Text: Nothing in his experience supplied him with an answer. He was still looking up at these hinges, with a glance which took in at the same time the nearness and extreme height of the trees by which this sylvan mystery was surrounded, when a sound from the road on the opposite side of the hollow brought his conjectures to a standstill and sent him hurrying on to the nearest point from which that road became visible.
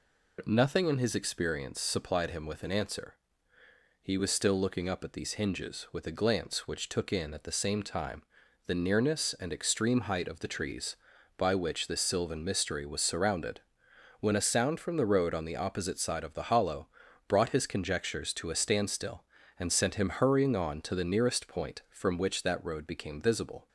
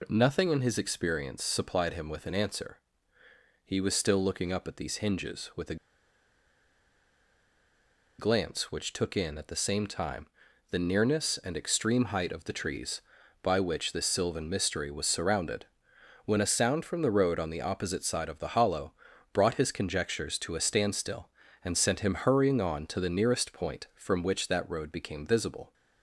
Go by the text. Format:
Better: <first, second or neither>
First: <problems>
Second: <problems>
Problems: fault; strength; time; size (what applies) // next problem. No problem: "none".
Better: first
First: pauses between "time" and "the"; at 8.2 s; 0.44 s long // pauses between "hollow" and "brought"; at 16.8 s; 0.40 s long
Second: pauses between "a" and "glance"; strong; at 5.7 s; 2.4 s long // pauses between "time" and "the"; at 10.2 s; 0.44 s long // pauses between "hollow" and "brought"; at 18.9 s; 0.40 s long